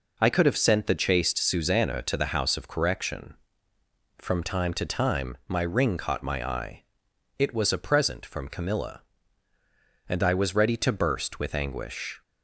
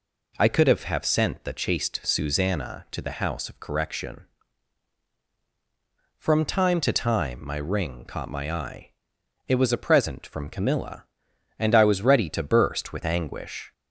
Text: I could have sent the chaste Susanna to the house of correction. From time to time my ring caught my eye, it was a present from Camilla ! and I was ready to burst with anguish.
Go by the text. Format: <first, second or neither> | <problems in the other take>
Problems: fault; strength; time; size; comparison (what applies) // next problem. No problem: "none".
first | says "have" twice; at 0.8 s